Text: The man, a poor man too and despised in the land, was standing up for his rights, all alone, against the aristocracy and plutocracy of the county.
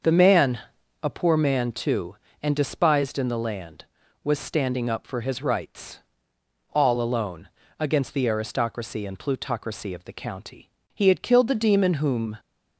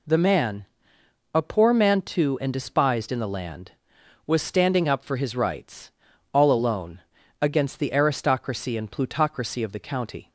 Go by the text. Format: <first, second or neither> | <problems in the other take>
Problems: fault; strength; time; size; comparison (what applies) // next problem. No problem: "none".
second | starts louder than the rest; until 1.5 s; 6.5 dB // goes on to say "He had killed the demon whom"; from 10.9 s on; 1.4 s long